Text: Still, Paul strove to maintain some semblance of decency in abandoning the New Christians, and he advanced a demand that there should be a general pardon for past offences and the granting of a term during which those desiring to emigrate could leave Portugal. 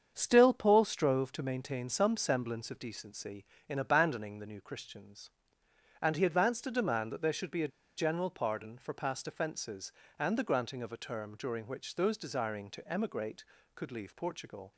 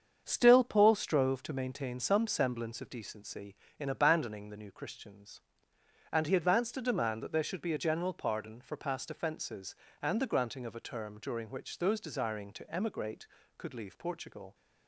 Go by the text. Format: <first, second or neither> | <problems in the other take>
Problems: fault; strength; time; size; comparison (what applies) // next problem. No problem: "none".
second | starts louder than the rest; strong; until 1.1 s; 7.5 dB; strong in the second // pauses between "a" and "general"; slight; at 7.7 s; 0.29 s long